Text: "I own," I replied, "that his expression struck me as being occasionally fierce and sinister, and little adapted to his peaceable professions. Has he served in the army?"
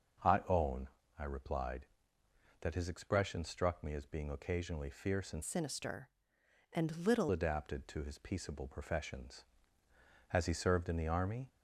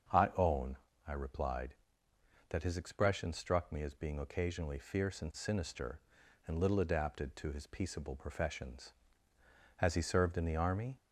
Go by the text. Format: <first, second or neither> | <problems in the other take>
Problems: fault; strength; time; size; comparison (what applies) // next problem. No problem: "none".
second | starts louder than the rest; noticeable; until 1.5 s; 6 dB; also in the second // changes voice from "sinister" to "little"; from 5.4 to 7.2 s; 1.8 s long